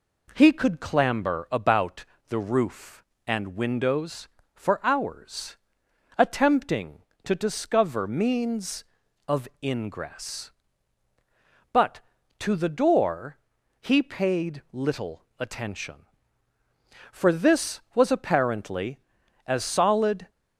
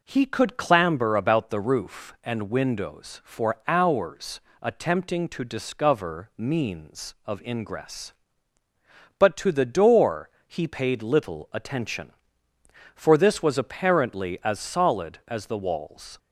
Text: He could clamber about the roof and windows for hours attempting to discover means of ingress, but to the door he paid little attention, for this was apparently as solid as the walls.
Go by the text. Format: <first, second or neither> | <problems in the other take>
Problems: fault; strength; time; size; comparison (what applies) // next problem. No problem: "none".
second | pauses between "about" and "the"; slight; at 2.0 s; 0.24 s long // pauses between "hours" and "attempting"; noticeable; at 5.5 s; 0.60 s long; slight in the second // pauses between "of" and "ingress"; slight; at 9.4 s; 0.16 s long // pauses between "door" and "he"; at 13.3 s; 0.42 s long; slight in the second // pauses between "little" and "attention"; slight; at 15.2 s; 0.16 s long // stops before "as the walls"; at 20.2 s